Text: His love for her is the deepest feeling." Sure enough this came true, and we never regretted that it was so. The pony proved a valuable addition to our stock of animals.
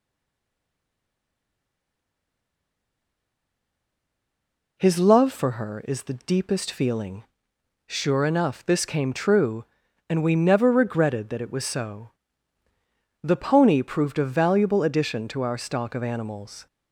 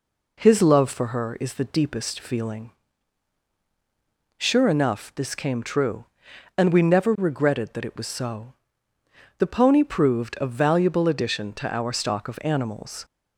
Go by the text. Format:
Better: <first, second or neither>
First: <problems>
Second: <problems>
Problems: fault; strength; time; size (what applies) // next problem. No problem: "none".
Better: second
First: stays silent before the first word; strong; until 4.7 s; 4.7 s long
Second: none